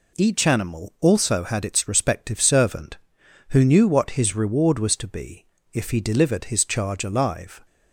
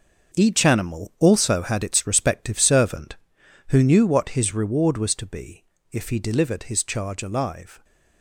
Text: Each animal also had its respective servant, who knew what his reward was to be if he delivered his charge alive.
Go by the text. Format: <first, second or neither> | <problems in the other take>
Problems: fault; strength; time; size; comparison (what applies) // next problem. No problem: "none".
first | gets quieter; strong; throughout; 9 dB // pauses between "be" and "if"; slight; at 5.6 s; 0.28 s long; slight in the first